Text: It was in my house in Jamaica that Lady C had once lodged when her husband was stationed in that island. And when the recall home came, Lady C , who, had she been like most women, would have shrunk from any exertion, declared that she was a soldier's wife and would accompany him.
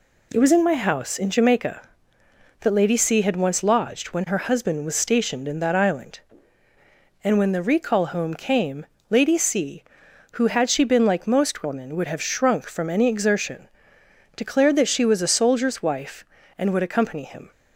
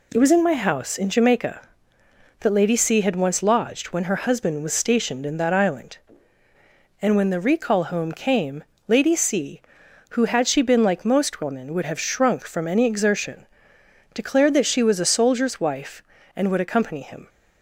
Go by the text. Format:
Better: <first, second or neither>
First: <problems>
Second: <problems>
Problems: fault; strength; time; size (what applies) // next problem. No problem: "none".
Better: neither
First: none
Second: none